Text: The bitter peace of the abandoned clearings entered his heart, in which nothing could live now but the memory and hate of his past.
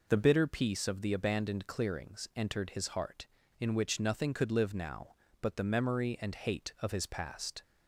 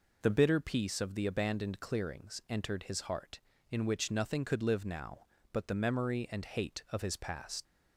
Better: first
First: none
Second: leaves "past" unfinished; at 7.6 s; 65 ms

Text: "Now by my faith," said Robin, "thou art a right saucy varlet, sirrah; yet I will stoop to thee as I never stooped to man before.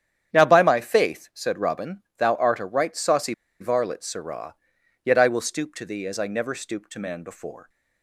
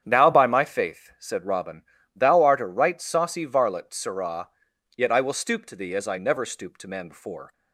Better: second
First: starts louder than the rest; strong; until 1.3 s; 9 dB // pauses between "saucy" and "varlet"; slight; at 3.3 s; 0.27 s long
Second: starts louder than the rest; strong; until 1.0 s; 8.5 dB

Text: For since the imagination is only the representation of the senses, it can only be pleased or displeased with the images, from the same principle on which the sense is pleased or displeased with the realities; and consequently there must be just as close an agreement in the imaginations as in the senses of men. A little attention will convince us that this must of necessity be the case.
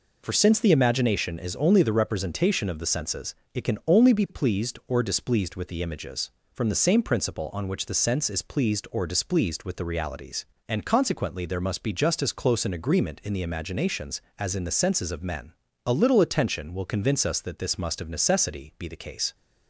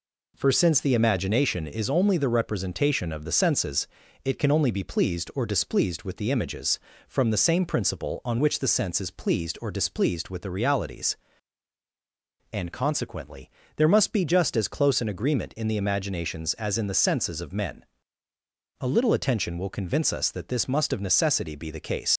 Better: first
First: none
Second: pauses between "consequently" and "there"; slight; at 13.4 s; 0.28 s long // leaves "case" unfinished; at 22.1 s; 85 ms

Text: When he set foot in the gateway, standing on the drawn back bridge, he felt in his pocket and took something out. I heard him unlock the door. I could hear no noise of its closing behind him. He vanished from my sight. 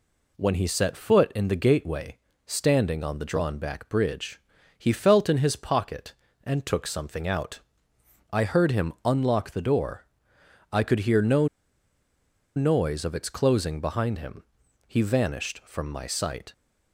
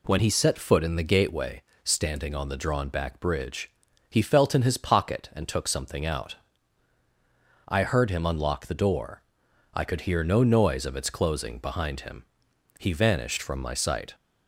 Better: second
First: pauses between "no" and "noise"; at 11.4 s; 1.0 s long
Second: none

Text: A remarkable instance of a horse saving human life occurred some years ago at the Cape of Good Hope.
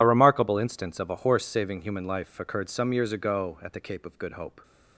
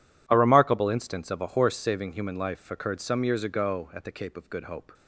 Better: second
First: loses the start of "A"; at 0.0 s; 35 ms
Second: none

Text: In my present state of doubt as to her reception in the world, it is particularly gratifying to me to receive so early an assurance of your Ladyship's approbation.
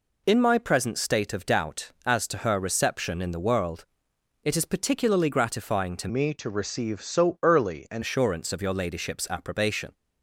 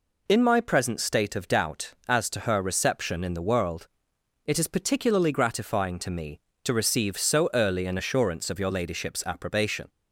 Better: second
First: changes voice from "me" to "an"; from 6.0 to 8.0 s; 2.0 s long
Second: none

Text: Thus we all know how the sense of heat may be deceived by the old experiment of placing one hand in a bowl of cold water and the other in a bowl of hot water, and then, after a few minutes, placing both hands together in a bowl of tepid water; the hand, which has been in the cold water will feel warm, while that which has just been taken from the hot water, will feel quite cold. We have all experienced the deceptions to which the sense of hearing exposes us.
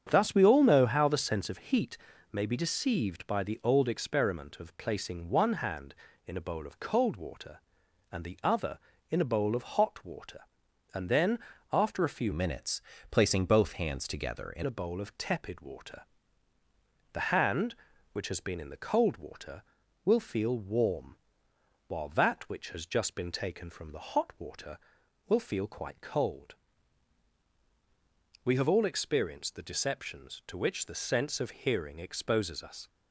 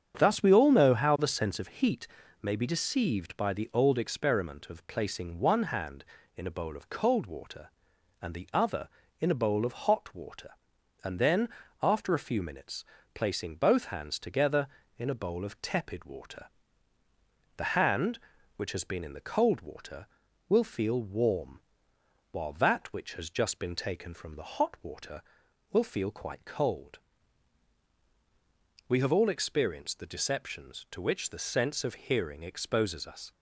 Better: second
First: starts louder than the rest; strong; until 1.1 s; 8 dB // pauses between "heat" and "may"; slight; at 1.9 s; 0.34 s long // changes voice from "minutes" to "in"; from 12.3 to 14.6 s; 2.3 s long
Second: starts louder than the rest; strong; until 1.2 s; 8 dB // pauses between "heat" and "may"; slight; at 2.0 s; 0.34 s long

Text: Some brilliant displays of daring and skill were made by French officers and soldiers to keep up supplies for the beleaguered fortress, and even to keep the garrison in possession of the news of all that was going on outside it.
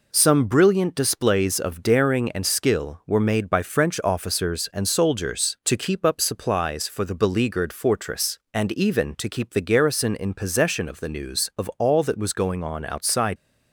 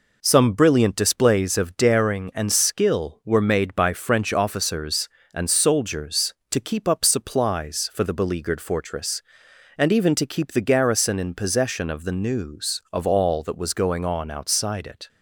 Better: second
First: stops before "it"; at 13.3 s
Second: none

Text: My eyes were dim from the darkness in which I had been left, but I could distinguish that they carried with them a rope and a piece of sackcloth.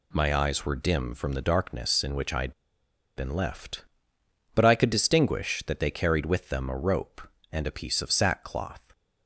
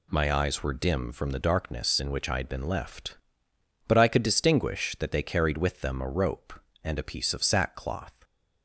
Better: second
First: pauses between "had" and "been"; noticeable; at 2.5 s; 0.65 s long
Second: none

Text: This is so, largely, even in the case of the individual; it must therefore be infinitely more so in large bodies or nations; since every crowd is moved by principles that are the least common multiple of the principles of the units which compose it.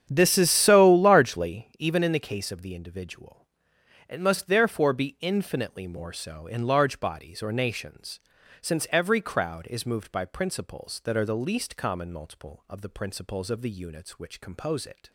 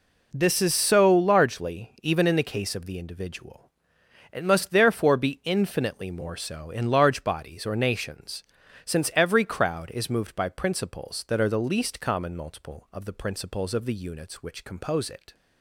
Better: second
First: starts louder than the rest; strong; until 1.7 s; 9 dB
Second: none

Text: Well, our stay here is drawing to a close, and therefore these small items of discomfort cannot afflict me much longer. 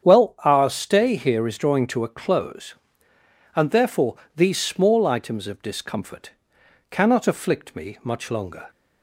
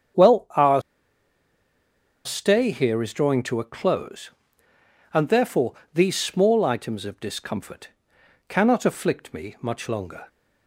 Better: first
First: starts louder than the rest; strong; until 1.0 s; 8 dB // pauses between "therefore" and "these"; slight; at 4.1 s; 0.18 s long // pauses between "discomfort" and "cannot"; noticeable; at 6.2 s; 0.60 s long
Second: starts louder than the rest; strong; until 2.6 s; 8 dB // pauses between "our" and "stay"; strong; at 0.8 s; 1.4 s long // pauses between "therefore" and "these"; slight; at 5.7 s; 0.18 s long // pauses between "discomfort" and "cannot"; noticeable; at 7.8 s; 0.60 s long

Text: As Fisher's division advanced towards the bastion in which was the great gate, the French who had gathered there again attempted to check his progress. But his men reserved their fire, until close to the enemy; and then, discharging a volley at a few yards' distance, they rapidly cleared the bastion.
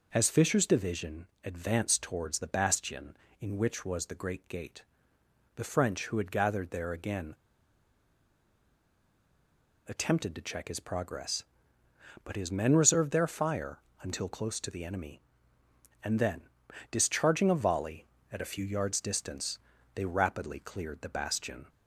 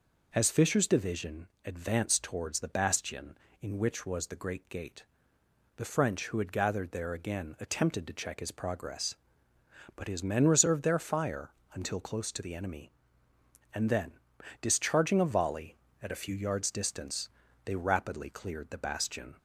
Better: second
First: pauses between "division" and "advanced"; slight; at 1.2 s; 0.18 s long // pauses between "again" and "attempted"; strong; at 7.3 s; 2.5 s long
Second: pauses between "division" and "advanced"; slight; at 1.4 s; 0.18 s long

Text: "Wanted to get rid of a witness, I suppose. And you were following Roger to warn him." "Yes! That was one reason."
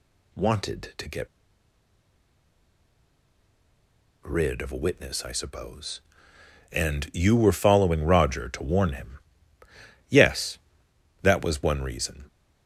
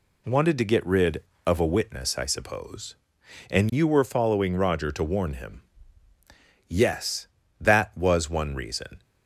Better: second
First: pauses between "get" and "rid"; strong; at 1.2 s; 2.9 s long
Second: none

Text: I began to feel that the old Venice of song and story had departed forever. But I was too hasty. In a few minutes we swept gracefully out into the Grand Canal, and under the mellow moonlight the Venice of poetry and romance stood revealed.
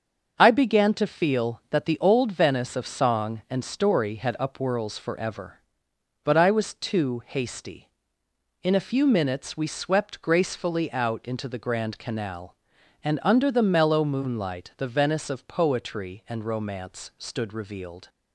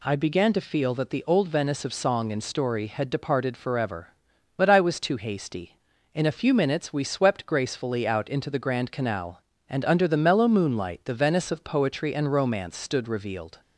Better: second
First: starts louder than the rest; until 1.3 s; 6.5 dB // says "upwhirls" for "departed"; at 4.3 s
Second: none

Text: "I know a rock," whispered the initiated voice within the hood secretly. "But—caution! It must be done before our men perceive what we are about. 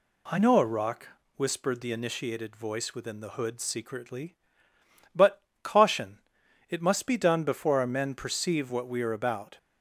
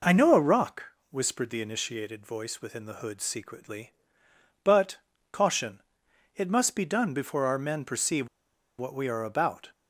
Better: first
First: none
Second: pauses between "perceive" and "what"; noticeable; at 8.2 s; 0.51 s long

